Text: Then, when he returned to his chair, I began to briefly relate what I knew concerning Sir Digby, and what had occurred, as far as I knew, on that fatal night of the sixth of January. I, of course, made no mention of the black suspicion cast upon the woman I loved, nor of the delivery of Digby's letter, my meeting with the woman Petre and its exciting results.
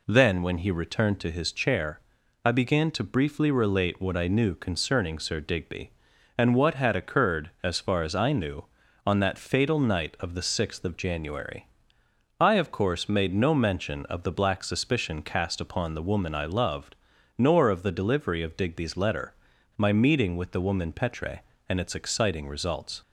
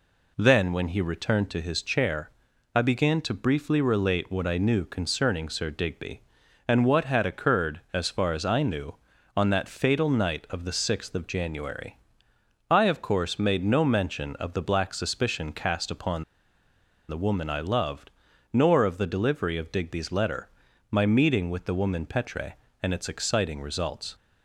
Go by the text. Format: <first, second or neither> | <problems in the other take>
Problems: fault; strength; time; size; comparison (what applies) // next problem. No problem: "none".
first | pauses between "upon" and "the"; noticeable; at 16.2 s; 0.84 s long